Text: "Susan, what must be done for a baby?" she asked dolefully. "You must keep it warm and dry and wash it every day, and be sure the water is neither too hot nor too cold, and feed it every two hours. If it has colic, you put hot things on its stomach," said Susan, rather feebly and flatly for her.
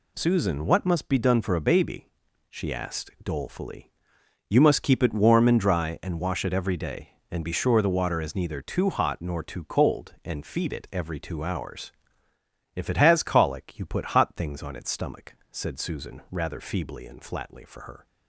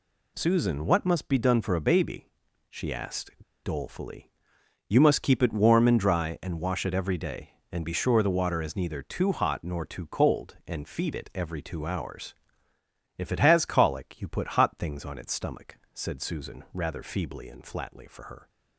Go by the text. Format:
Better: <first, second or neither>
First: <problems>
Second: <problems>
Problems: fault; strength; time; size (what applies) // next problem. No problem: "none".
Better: first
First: none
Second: pauses between "asked" and "dolefully"; slight; at 3.3 s; 0.33 s long